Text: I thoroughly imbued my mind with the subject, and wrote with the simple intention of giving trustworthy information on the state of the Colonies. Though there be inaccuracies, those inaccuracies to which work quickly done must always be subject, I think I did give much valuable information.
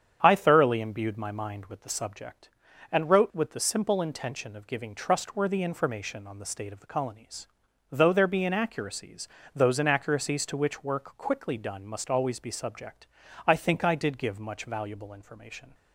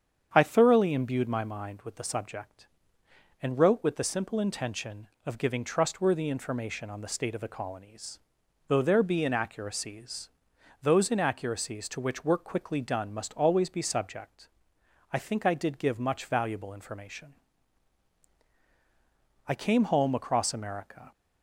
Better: first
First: starts louder than the rest; strong; until 1.2 s; 8.5 dB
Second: starts louder than the rest; strong; until 1.3 s; 8 dB // goes on to say "I came home across America"; from 19.4 s on; 1.6 s long

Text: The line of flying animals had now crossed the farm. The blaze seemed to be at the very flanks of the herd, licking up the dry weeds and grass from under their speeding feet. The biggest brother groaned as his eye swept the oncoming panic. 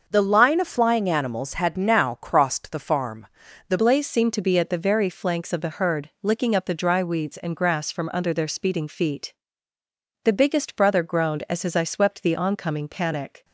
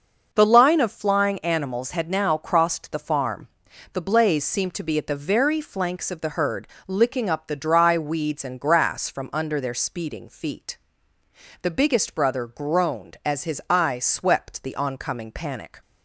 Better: second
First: starts louder than the rest; until 1.0 s; 6.5 dB // changes voice at "blaze"; from 3.7 s on; 9.7 s long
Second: none

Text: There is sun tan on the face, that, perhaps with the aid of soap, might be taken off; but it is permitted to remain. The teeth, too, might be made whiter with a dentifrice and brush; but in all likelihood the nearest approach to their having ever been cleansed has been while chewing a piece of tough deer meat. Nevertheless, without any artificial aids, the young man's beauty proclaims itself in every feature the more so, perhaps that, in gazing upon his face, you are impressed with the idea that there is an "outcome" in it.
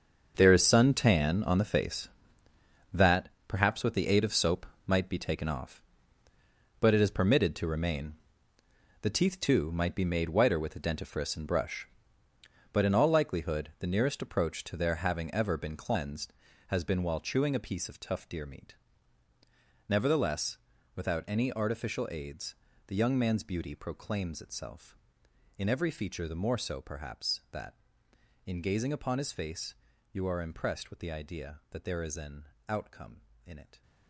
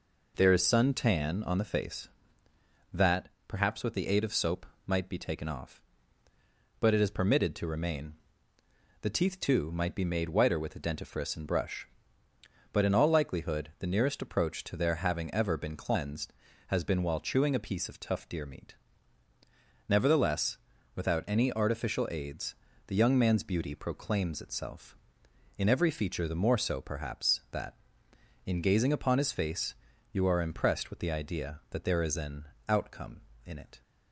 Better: second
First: gets quieter; strong; throughout; 13 dB // pauses between "an" and "outcome"; slight; at 32.4 s; 0.22 s long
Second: pauses between "an" and "outcome"; slight; at 32.4 s; 0.22 s long

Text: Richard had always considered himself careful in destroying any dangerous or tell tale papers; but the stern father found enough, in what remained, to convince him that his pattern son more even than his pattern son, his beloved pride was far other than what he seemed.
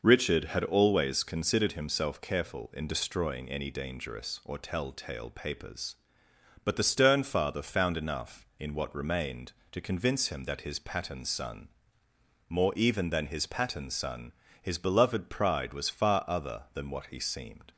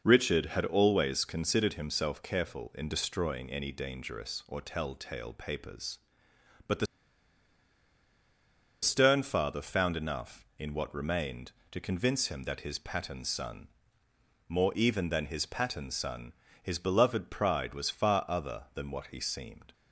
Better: first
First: pauses between "son" and "more"; noticeable; at 11.6 s; 0.80 s long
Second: pauses between "the" and "stern"; strong; at 6.8 s; 1.9 s long // pauses between "son" and "more"; noticeable; at 13.6 s; 0.80 s long

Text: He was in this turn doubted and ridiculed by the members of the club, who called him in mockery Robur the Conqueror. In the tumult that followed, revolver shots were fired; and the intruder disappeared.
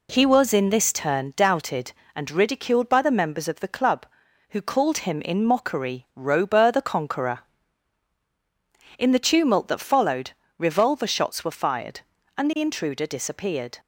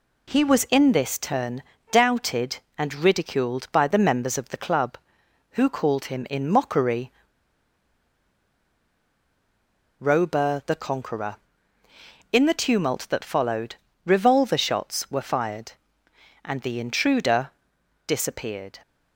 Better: first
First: none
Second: pauses between "turn" and "doubted"; slight; at 1.6 s; 0.28 s long // pauses between "mockery" and "Robur"; strong; at 7.1 s; 2.8 s long // pauses between "intruder" and "disappeared"; noticeable; at 17.4 s; 0.56 s long

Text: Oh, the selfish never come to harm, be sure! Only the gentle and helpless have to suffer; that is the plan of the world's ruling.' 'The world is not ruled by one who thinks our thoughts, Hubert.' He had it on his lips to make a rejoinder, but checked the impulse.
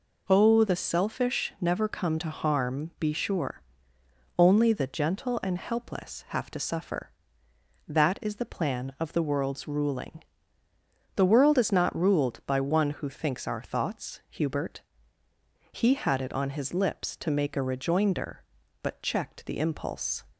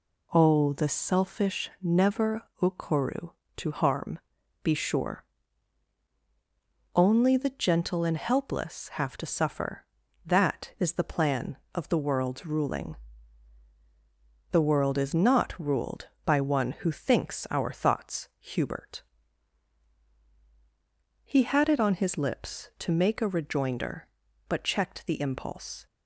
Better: first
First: none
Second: says "okoru" for "come"; at 2.6 s

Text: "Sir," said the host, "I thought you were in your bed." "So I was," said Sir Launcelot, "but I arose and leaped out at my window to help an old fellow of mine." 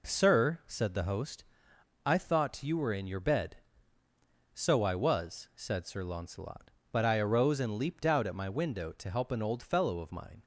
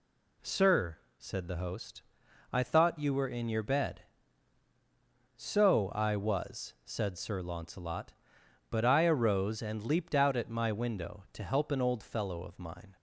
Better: neither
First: none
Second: none

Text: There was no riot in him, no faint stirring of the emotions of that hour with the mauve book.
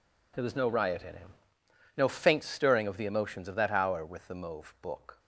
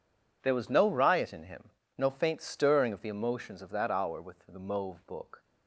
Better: neither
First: none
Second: none

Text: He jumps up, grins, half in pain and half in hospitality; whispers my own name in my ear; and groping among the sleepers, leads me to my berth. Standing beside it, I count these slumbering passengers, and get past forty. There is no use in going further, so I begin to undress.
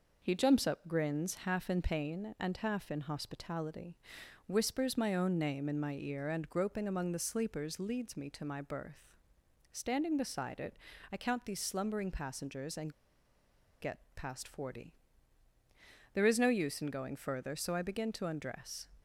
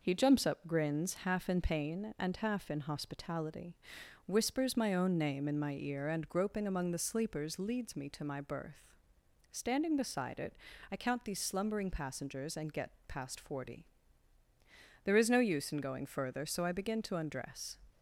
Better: second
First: pauses between "and" and "get"; noticeable; at 12.9 s; 0.88 s long // pauses between "get" and "past"; slight; at 13.9 s; 0.16 s long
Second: pauses between "get" and "past"; slight; at 12.9 s; 0.16 s long

